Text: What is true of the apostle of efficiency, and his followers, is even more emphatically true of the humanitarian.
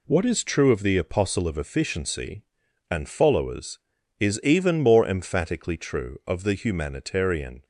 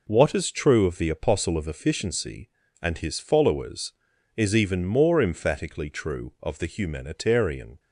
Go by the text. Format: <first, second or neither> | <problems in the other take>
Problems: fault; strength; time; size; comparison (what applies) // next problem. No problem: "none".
second | skips "his"; at 3.0 s